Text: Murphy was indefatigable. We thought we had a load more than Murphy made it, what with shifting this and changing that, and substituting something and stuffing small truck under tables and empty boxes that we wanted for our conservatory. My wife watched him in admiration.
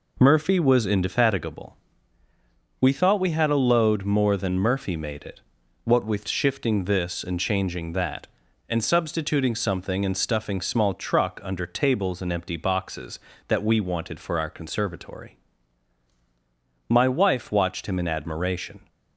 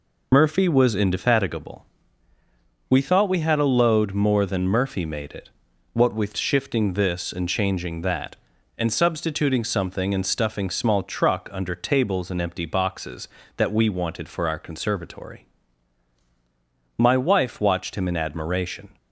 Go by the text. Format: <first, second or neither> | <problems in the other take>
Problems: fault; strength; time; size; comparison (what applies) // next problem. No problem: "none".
first | loses the start of "Murphy"; at 0.3 s; 65 ms